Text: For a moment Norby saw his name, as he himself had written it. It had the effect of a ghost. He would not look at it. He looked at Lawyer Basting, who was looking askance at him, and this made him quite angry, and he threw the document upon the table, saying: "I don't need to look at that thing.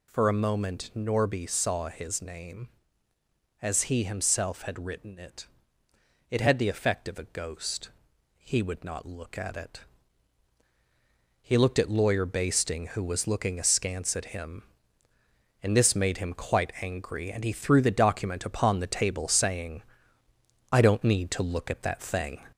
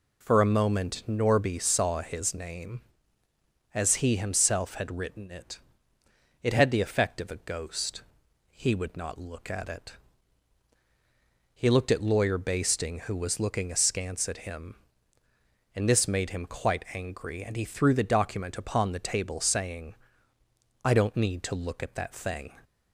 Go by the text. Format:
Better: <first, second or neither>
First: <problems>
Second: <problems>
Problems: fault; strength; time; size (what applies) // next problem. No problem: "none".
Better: second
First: gets louder; slight; throughout; 3 dB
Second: none